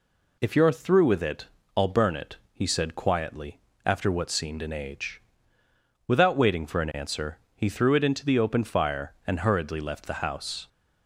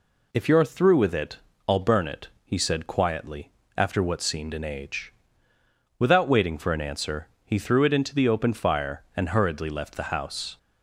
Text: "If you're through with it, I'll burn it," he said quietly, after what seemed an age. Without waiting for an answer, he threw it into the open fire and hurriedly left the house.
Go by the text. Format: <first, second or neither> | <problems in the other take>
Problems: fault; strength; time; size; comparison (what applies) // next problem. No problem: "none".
neither | none